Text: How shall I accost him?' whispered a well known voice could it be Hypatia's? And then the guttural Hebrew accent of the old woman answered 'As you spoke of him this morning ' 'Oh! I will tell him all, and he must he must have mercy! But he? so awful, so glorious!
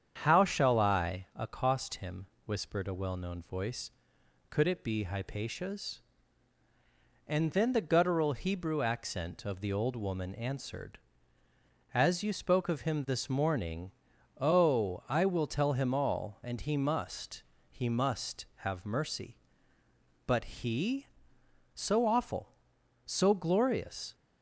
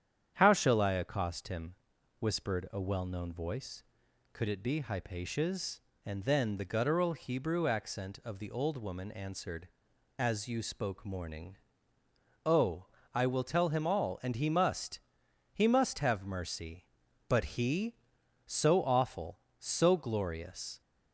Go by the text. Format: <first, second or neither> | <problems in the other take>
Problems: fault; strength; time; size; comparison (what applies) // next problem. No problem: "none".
first | starts louder than the rest; strong; until 1.3 s; 9 dB; strong in the first // skips "of him this"; at 11.0 s // pauses between "must" and "he"; noticeable; at 15.0 s; 0.52 s long; slight in the first